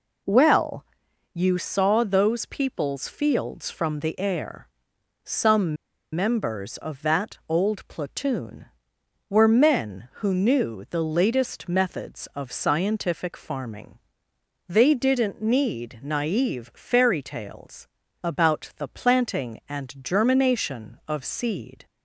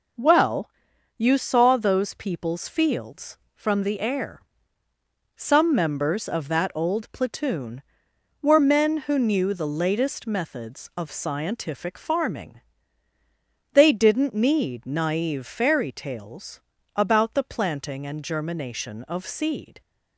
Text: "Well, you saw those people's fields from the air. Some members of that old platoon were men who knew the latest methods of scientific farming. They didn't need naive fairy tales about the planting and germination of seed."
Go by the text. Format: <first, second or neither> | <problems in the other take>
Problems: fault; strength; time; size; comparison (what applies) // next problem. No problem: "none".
second | pauses between "Some" and "members"; at 5.7 s; 0.39 s long // pauses between "tales" and "about"; slight; at 17.8 s; 0.36 s long; slight in the second